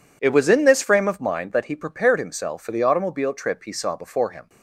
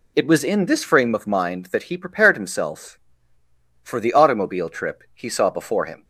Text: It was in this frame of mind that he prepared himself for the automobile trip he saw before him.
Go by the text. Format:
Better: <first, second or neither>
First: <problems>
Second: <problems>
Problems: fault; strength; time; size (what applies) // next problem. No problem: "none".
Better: neither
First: none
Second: none